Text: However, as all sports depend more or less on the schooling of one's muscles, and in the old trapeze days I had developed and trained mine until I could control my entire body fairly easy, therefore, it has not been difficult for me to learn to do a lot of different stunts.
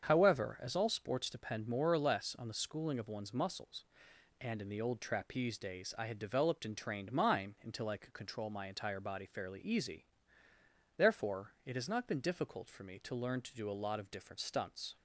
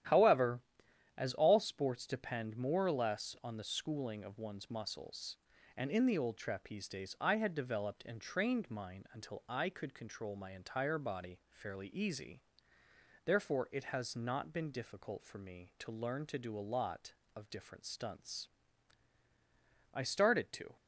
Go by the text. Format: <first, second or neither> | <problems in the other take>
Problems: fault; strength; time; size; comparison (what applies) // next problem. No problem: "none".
first | starts louder than the rest; strong; until 1.6 s; 11.5 dB; strong in the first // goes on to say "I started to"; noticeable; from 19.9 s on; 0.84 s long